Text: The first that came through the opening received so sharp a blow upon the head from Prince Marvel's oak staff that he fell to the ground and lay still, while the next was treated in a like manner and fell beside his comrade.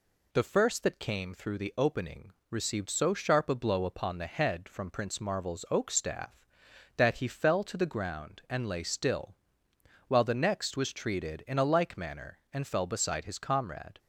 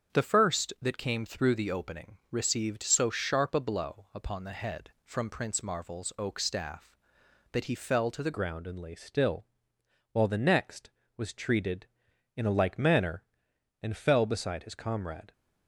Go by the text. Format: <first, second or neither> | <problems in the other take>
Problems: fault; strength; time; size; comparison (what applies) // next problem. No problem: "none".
first | starts louder than the rest; strong; until 1.2 s; 7.5 dB // pauses between "opening" and "received"; slight; at 2.1 s; 0.16 s long; slight in the first // changes voice at "ground"; from 8.3 s on; 7.0 s long